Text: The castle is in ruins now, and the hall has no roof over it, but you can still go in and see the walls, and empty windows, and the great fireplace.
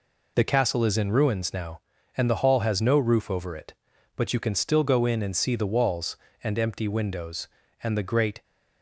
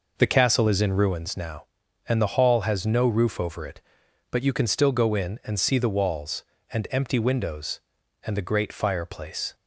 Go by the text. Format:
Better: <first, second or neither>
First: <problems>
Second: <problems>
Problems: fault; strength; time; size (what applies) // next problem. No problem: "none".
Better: second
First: stops before "fireplace"; at 8.4 s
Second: none